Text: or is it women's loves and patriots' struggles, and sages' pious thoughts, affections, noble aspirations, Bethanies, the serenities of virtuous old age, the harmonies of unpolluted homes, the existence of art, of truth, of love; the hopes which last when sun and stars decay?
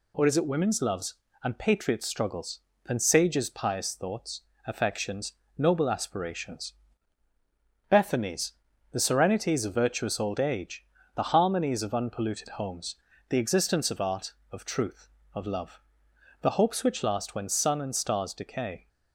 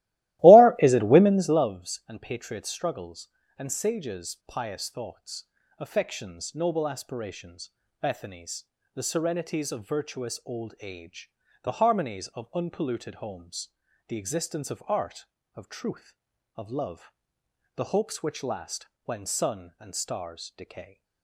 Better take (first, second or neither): first